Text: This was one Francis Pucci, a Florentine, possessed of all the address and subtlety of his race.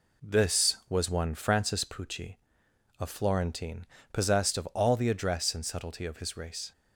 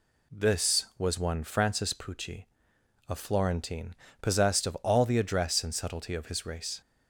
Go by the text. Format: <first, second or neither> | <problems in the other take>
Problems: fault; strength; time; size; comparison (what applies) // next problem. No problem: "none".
second | gets quieter; noticeable; throughout; 4 dB